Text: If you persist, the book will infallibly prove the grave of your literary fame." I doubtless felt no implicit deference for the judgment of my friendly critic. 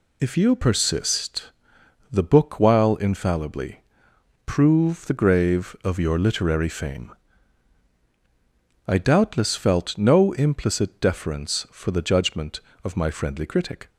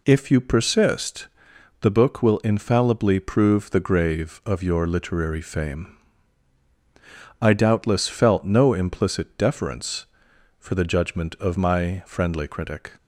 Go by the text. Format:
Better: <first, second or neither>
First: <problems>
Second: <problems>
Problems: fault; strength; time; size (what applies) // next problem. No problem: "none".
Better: second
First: says "while" for "will"; at 2.5 s // pauses between "infallibly" and "prove"; noticeable; at 3.7 s; 0.66 s long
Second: none